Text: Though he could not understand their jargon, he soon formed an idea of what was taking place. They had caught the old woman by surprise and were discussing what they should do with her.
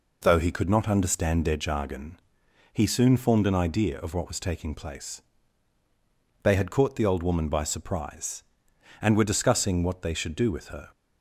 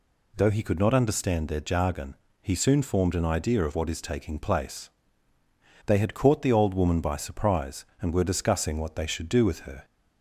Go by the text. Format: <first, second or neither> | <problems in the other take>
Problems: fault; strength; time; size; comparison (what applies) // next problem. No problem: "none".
first | says "is" for "was"; at 3.8 s